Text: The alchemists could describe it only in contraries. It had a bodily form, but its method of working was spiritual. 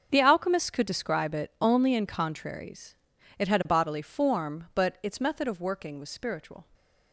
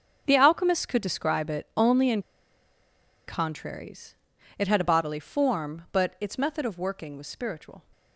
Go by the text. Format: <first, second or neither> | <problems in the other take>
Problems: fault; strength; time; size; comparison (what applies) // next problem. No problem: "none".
first | starts louder than the rest; until 1.2 s; 6.5 dB; also in the first // pauses between "in" and "contraries"; at 2.1 s; 1.0 s long